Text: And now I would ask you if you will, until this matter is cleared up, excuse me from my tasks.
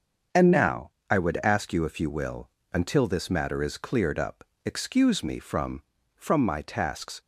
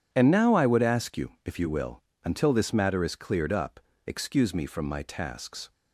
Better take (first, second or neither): second